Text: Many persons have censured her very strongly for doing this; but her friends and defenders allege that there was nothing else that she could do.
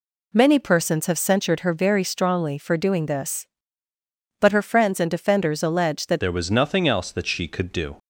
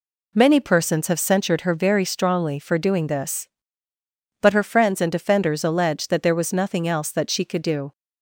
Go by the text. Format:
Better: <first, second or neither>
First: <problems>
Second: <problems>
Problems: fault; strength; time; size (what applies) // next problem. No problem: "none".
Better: second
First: changes voice at "there"; from 6.2 s on; 1.7 s long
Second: none